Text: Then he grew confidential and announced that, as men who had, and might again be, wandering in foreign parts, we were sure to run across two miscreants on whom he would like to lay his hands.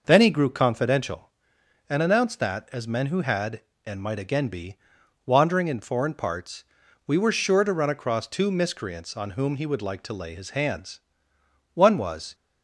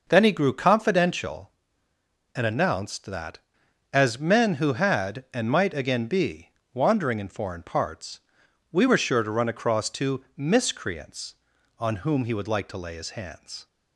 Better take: second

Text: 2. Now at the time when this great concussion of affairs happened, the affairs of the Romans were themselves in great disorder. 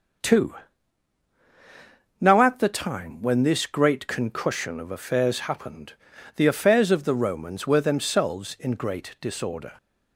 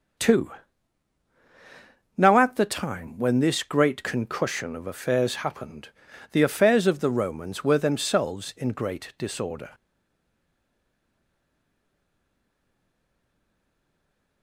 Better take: first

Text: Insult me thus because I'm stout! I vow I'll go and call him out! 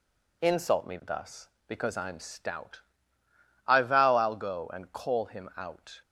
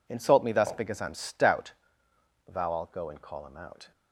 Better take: first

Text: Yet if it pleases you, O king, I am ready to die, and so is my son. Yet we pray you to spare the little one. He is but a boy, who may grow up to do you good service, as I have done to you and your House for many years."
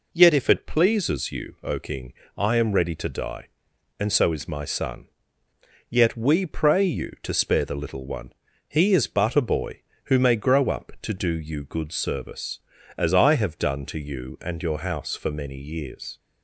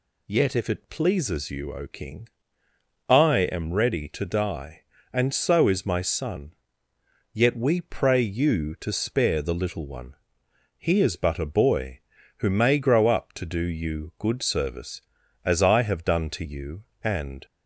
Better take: first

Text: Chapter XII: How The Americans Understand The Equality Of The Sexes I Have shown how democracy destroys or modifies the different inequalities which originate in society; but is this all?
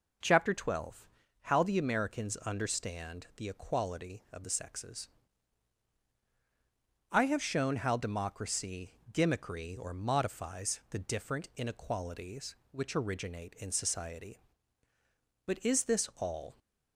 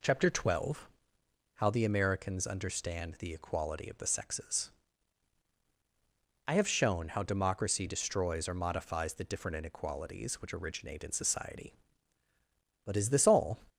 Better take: second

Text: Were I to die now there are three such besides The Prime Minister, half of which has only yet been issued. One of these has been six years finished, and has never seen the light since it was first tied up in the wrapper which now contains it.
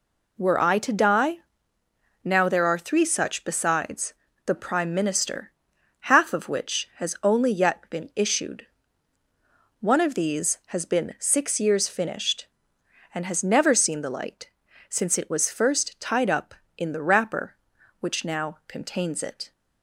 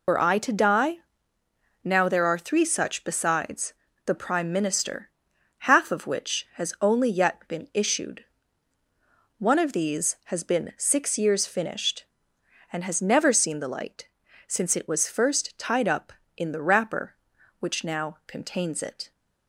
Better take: first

